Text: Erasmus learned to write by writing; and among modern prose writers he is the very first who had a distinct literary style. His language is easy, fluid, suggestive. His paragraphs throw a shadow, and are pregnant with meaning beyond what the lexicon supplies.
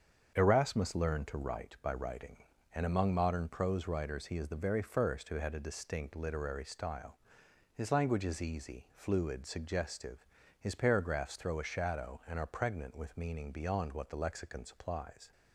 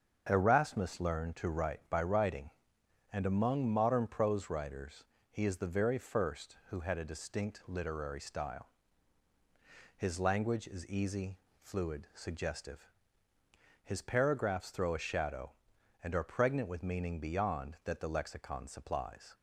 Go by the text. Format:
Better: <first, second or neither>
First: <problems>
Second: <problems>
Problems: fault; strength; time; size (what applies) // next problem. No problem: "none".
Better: first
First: starts louder than the rest; strong; until 1.3 s; 7 dB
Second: starts louder than the rest; until 1.3 s; 7 dB // pauses between "writers" and "he"; slight; at 5.0 s; 0.26 s long // says "that" for "what"; at 17.8 s